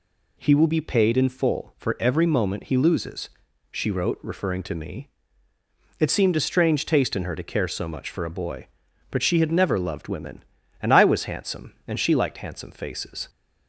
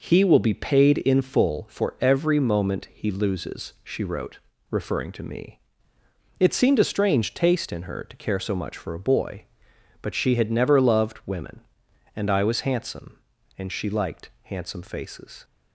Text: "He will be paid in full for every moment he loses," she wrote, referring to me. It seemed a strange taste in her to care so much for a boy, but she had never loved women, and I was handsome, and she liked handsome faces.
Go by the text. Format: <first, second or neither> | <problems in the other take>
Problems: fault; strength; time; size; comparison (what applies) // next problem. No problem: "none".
neither | none